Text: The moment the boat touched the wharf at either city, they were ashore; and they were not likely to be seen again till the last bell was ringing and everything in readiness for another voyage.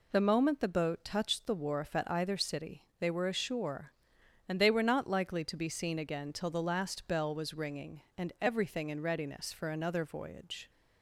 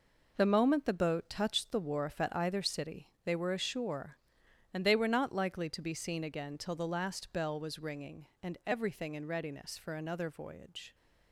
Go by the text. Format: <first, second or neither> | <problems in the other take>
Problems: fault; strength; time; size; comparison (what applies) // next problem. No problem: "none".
first | gets quieter; strong; throughout; 9 dB